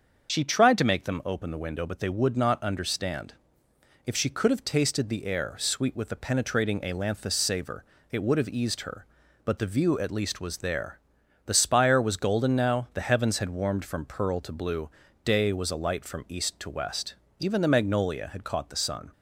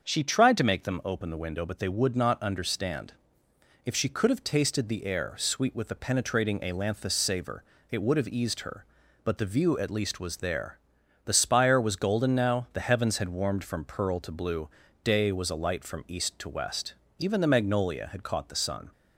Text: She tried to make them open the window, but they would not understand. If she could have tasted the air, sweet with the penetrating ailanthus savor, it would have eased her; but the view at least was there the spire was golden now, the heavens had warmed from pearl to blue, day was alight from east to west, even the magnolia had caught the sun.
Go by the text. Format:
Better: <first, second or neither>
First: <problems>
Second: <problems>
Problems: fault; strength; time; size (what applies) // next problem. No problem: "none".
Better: second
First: loses the start of "She"; at 0.2 s; 60 ms // starts louder than the rest; until 1.3 s; 7 dB // pauses between "there" and "the"; noticeable; at 10.9 s; 0.46 s long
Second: starts louder than the rest; until 1.0 s; 6.5 dB // pauses between "there" and "the"; noticeable; at 10.7 s; 0.46 s long